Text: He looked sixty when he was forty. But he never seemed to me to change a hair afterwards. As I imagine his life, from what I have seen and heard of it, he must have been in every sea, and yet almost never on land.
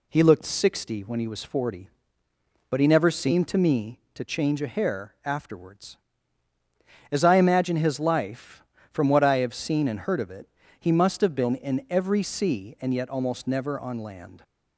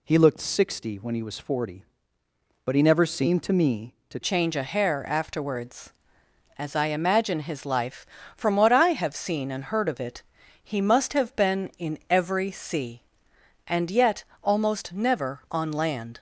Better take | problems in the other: first | changes voice at "change"; from 4.2 s on; 11.9 s long // pauses between "yet" and "almost"; slight; at 14.2 s; 0.18 s long

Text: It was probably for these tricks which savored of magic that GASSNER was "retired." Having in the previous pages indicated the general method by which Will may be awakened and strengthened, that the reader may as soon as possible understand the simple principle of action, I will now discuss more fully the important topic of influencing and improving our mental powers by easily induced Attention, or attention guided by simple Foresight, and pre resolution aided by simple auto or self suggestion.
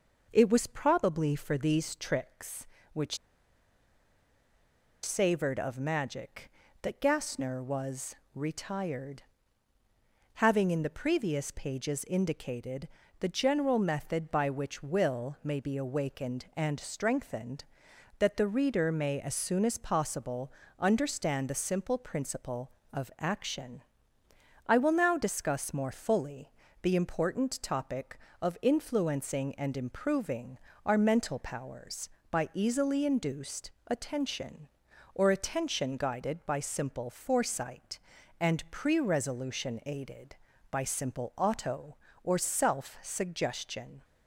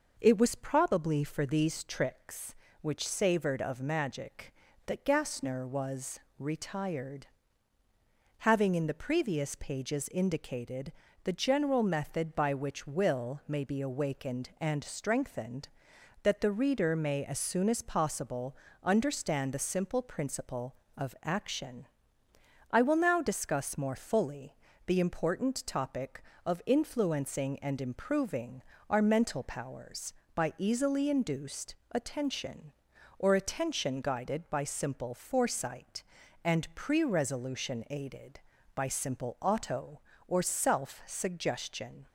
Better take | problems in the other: second | pauses between "which" and "savored"; strong; at 3.1 s; 1.8 s long // pauses between "was" and "retired"; slight; at 8.1 s; 0.22 s long; slight in the second // pauses between "indicated" and "the"; slight; at 12.8 s; 0.32 s long; slight in the second // pauses between "possible" and "understand"; slight; at 20.5 s; 0.26 s long; slight in the second // pauses between "fully" and "the"; slight; at 26.5 s; 0.30 s long; slight in the second // pauses between "improving" and "our"; slight; at 30.5 s; 0.26 s long; slight in the second // pauses between "induced" and "Attention"; slight; at 33.7 s; 0.16 s long; slight in the second

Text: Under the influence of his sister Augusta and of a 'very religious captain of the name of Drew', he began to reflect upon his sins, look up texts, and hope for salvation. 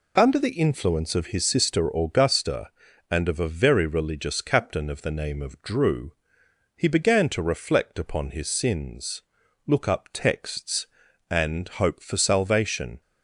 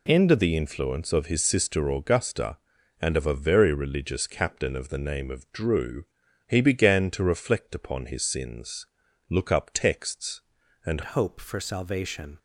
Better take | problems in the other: first | changes voice at "hope"; from 11.0 s on; 1.3 s long

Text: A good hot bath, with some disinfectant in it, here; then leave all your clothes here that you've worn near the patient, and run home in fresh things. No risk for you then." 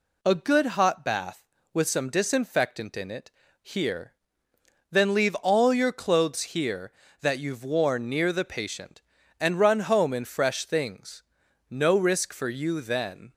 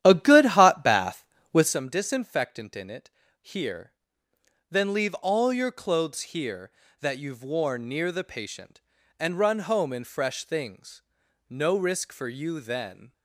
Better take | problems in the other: first | starts louder than the rest; strong; until 1.8 s; 11.5 dB

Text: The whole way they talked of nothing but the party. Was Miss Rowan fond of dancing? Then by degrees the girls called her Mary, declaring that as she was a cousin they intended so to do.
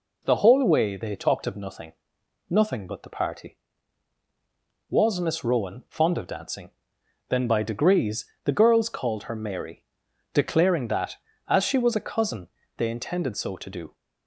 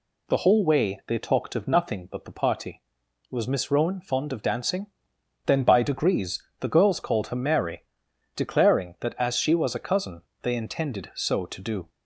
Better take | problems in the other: second | says "nothing" twice; at 2.4 s // pauses between "degrees" and "the"; slight; at 8.2 s; 0.18 s long; slight in the second // pauses between "cousin" and "they"; slight; at 12.4 s; 0.28 s long; slight in the second

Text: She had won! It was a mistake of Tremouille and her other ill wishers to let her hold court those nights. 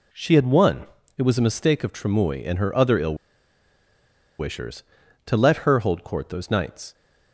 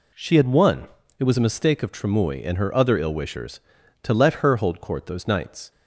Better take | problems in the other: second | pauses between "ill" and "wishers"; at 3.1 s; 1.2 s long

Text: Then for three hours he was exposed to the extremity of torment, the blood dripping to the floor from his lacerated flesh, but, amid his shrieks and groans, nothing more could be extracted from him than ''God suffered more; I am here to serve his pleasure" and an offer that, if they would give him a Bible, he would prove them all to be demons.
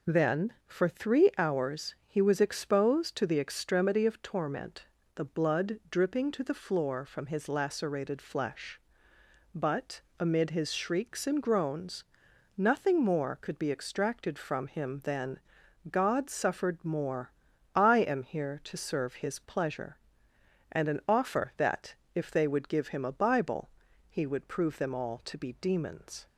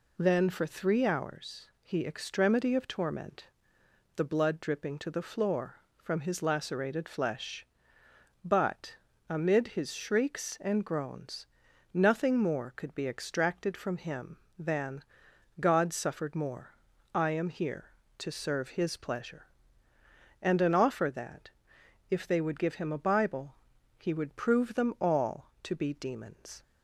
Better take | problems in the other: first | skips "was exposed to the"; at 2.0 s // pauses between "than" and "God"; noticeable; at 15.0 s; 0.58 s long; noticeable in the first

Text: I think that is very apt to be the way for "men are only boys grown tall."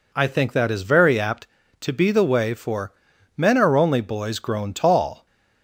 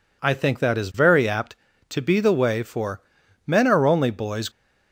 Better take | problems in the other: first | pauses between "for" and "men"; noticeable; at 3.0 s; 0.46 s long; also in the first // stops before "grown tall"; at 4.4 s

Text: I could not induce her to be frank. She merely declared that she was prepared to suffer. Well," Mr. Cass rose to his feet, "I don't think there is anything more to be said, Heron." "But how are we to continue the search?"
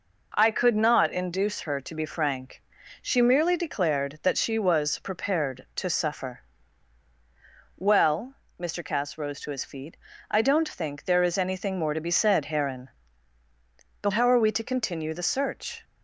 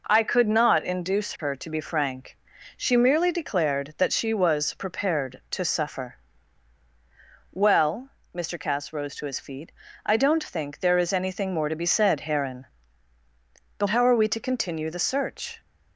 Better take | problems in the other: neither | none

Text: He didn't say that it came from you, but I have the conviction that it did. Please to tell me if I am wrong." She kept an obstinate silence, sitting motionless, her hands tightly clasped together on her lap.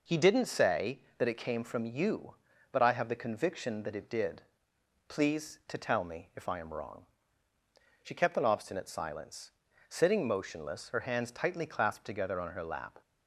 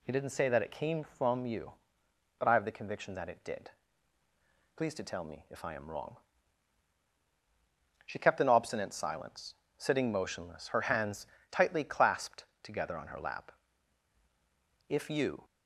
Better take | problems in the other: first | pauses between "hands" and "tightly"; slight; at 11.2 s; 0.26 s long // pauses between "clasped" and "together"; slight; at 12.4 s; 0.18 s long // goes on to say "If you"; from 14.8 s on; 0.56 s long

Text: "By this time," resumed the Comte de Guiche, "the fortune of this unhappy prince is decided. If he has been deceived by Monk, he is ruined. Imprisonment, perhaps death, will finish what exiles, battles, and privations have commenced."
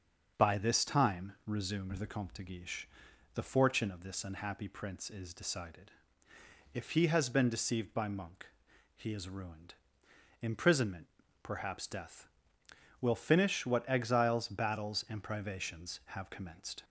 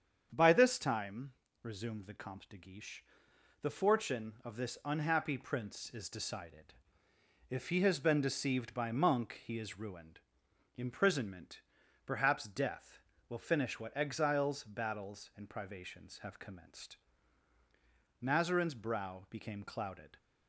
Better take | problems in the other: first | starts louder than the rest; strong; until 1.3 s; 7.5 dB; also in the first // goes on to say "Mazarin's brow became clouded"; strong; from 18.1 s on; 1.9 s long

